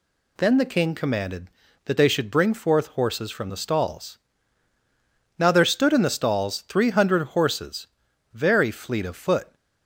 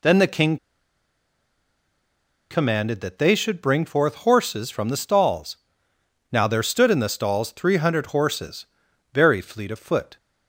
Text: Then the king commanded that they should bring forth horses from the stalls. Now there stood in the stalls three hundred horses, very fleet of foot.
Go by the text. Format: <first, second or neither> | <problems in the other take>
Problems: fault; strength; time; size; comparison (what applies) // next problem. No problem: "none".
first | pauses between "king" and "commanded"; strong; at 0.5 s; 1.9 s long